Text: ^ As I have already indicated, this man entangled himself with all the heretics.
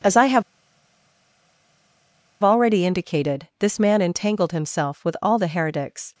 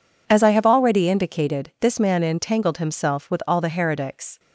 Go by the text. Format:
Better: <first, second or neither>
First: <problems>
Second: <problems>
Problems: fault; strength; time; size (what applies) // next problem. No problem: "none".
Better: second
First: pauses between "have" and "already"; strong; at 0.4 s; 1.9 s long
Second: none